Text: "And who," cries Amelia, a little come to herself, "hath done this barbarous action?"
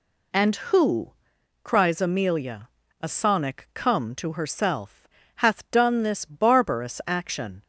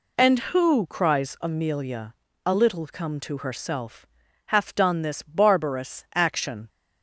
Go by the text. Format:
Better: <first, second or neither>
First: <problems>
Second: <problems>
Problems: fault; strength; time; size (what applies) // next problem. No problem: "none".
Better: second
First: says "sonic" for "little"; at 3.0 s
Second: none